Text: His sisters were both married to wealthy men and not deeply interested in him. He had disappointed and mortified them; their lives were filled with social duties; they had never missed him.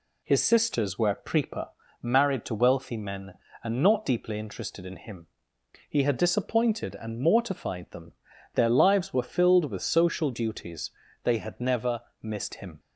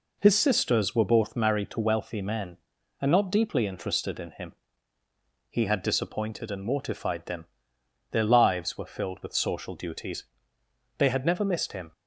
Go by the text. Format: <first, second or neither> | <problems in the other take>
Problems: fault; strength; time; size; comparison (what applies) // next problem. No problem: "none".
second | says "prepa" for "both"; at 1.1 s // pauses between "never" and "missed"; slight; at 12.0 s; 0.18 s long